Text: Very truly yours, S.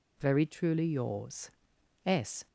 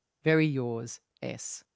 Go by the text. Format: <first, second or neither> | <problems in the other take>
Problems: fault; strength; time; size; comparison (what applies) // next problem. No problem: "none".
first | skips "truly"; at 0.4 s